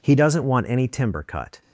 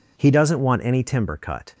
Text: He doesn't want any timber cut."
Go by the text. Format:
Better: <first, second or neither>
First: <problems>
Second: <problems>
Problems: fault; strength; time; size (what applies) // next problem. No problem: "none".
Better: neither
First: none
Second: none